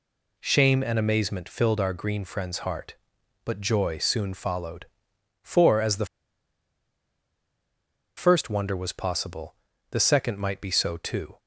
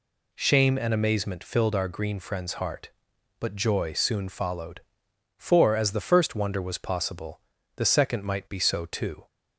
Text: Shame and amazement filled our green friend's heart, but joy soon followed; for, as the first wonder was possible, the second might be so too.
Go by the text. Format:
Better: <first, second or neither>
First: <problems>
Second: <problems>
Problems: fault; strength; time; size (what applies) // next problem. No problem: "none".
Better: second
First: pauses between "the" and "first"; strong; at 6.0 s; 2.1 s long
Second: none